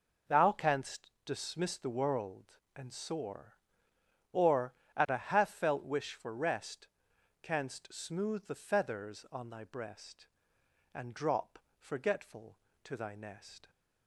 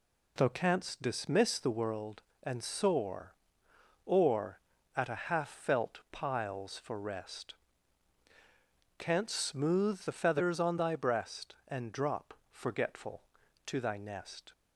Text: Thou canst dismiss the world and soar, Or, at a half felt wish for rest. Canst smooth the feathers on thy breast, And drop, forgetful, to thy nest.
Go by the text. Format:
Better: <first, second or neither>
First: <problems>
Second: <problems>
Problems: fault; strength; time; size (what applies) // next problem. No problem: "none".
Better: first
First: none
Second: says "piles" for "wish"; at 6.1 s